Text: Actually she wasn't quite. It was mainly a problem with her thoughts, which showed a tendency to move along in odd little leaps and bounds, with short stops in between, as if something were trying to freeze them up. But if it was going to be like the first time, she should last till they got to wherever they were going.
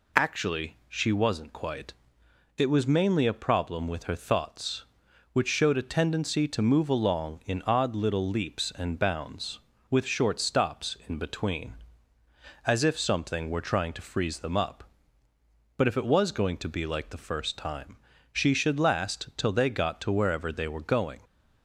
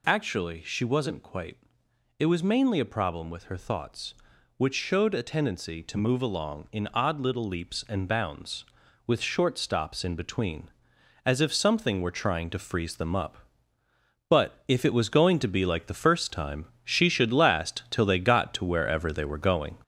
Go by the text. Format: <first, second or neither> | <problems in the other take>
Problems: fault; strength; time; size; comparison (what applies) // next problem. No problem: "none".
first | gets louder; noticeable; throughout; 4.5 dB